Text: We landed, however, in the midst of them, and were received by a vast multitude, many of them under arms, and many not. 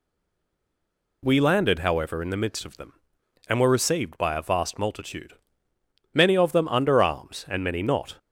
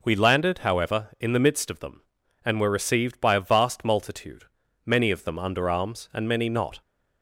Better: second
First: stays silent before the first word; noticeable; until 1.2 s; 1.2 s long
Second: none

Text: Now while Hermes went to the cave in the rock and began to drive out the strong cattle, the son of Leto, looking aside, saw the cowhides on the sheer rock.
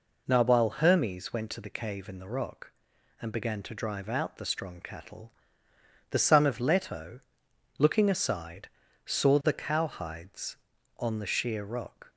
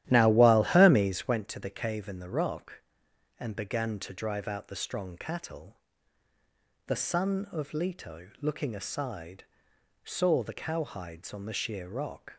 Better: first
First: none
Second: starts louder than the rest; strong; until 1.4 s; 12.5 dB

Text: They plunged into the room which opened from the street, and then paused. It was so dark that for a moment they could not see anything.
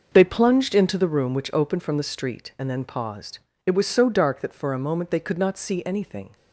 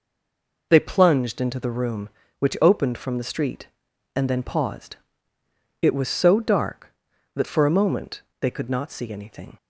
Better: first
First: none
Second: stays silent before the first word; slight; until 0.7 s; 0.7 s long // pauses between "moment" and "they"; slight; at 8.2 s; 0.18 s long

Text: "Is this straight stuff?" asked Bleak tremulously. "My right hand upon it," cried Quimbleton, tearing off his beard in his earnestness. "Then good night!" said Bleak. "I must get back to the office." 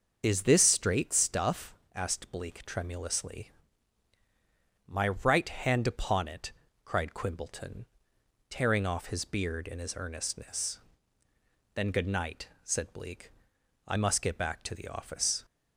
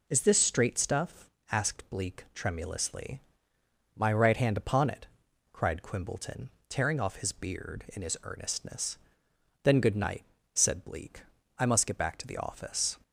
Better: second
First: loses the start of "Is"; at 0.2 s; 25 ms // starts louder than the rest; until 1.2 s; 6.5 dB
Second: none

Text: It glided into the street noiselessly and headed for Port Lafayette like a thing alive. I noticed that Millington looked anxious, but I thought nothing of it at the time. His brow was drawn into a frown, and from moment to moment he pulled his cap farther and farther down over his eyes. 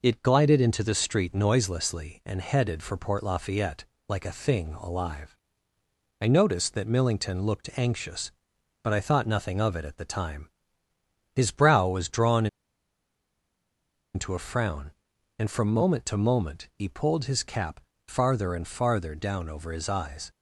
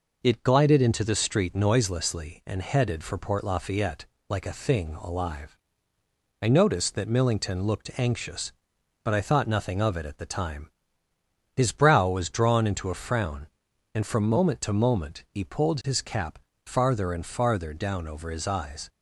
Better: second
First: pauses between "Lafayette" and "like"; slight; at 3.8 s; 0.24 s long // pauses between "drawn" and "into"; strong; at 12.4 s; 1.6 s long // pauses between "cap" and "farther"; slight; at 17.7 s; 0.26 s long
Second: pauses between "Lafayette" and "like"; slight; at 4.0 s; 0.24 s long // pauses between "cap" and "farther"; slight; at 16.3 s; 0.26 s long

